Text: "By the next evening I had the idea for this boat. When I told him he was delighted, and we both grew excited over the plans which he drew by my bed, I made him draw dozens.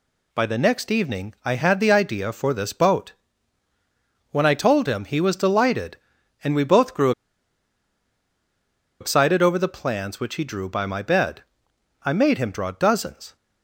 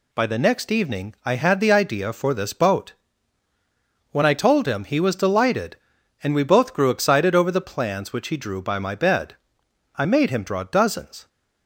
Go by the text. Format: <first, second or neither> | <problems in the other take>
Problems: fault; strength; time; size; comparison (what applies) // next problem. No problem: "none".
second | pauses between "grew" and "excited"; strong; at 7.1 s; 1.8 s long